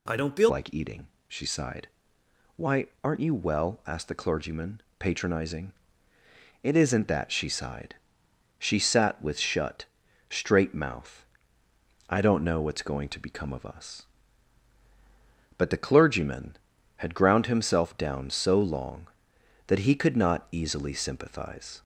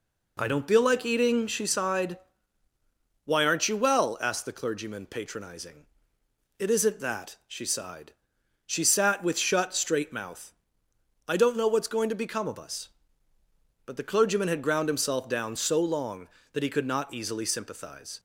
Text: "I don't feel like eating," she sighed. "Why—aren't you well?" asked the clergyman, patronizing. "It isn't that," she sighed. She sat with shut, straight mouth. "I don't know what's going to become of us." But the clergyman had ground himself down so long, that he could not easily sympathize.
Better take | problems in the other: second | changes voice at "like"; from 0.4 s on; 21.4 s long

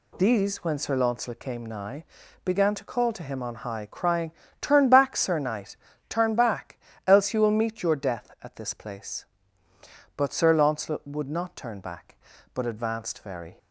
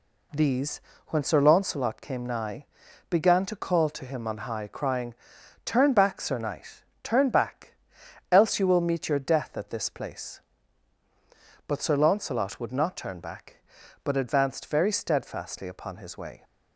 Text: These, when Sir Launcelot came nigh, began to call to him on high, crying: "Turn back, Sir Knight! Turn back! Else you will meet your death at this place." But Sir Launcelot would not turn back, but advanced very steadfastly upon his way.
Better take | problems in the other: second | stops before "steadfastly upon his way"; at 13.5 s

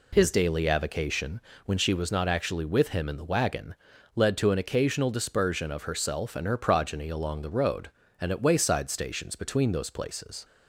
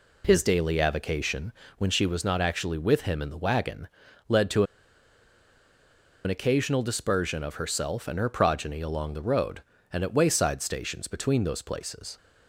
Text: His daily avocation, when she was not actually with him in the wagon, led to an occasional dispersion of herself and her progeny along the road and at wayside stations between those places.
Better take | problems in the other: first | pauses between "to" and "an"; strong; at 4.6 s; 1.6 s long

